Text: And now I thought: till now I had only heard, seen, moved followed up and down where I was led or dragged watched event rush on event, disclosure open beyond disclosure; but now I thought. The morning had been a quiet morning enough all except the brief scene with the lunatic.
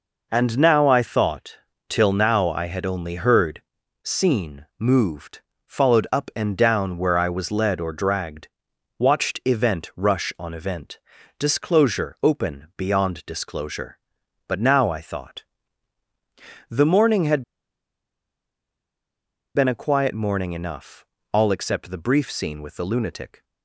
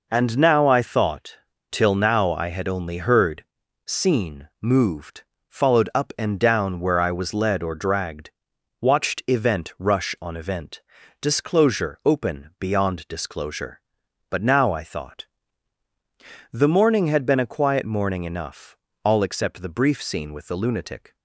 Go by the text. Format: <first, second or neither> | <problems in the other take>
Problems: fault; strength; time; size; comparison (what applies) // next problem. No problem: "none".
second | pauses between "moved" and "followed"; slight; at 5.4 s; 0.26 s long; slight in the second // pauses between "dragged" and "watched"; noticeable; at 8.4 s; 0.50 s long; noticeable in the second // pauses between "had" and "been"; strong; at 17.4 s; 2.1 s long // pauses between "enough" and "all"; slight; at 21.0 s; 0.30 s long; slight in the second